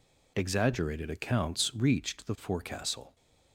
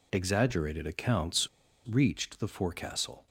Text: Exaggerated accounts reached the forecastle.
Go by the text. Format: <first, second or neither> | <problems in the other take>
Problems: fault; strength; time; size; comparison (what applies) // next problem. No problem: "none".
first | pauses between "accounts" and "reached"; at 1.4 s; 0.40 s long